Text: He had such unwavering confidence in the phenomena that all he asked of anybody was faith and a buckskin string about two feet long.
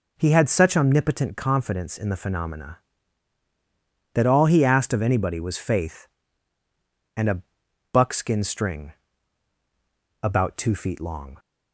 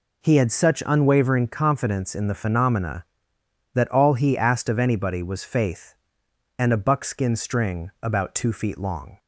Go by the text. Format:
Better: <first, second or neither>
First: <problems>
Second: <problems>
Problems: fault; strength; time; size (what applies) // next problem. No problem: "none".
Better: second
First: says "omnipotent" for "unwavering"; at 0.7 s // pauses between "a" and "buckskin"; noticeable; at 7.4 s; 0.50 s long // pauses between "string" and "about"; strong; at 8.9 s; 1.3 s long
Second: none